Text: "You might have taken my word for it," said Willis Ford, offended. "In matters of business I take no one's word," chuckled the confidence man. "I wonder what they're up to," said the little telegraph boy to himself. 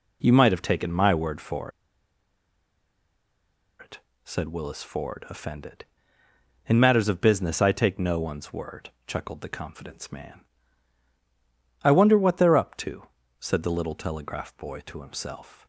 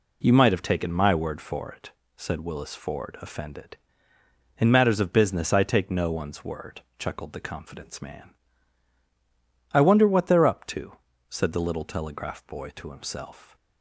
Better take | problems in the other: second | pauses between "for" and "it"; strong; at 1.7 s; 2.0 s long

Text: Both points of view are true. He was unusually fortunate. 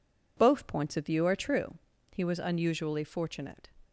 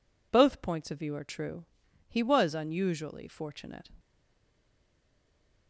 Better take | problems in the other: first | stays silent after the last word; noticeable; from 3.9 s on; 1.7 s long

